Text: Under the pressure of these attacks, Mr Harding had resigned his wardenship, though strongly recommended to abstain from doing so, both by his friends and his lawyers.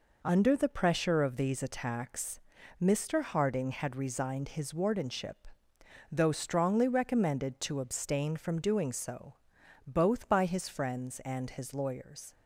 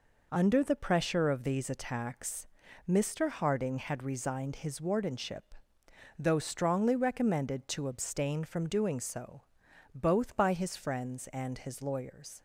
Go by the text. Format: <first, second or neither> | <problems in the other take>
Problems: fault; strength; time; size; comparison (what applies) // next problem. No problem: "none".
neither | none